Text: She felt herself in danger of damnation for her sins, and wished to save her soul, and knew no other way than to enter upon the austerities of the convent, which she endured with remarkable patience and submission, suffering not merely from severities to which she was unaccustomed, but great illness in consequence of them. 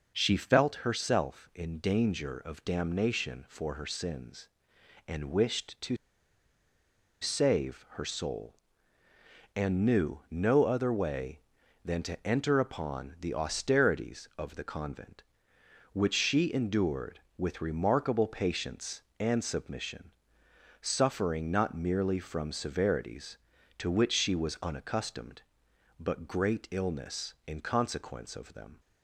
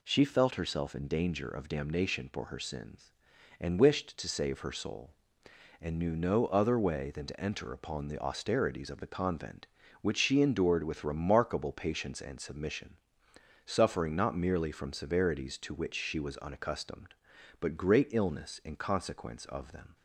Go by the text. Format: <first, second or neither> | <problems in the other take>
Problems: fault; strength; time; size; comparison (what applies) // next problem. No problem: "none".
second | pauses between "to" and "save"; strong; at 5.9 s; 1.2 s long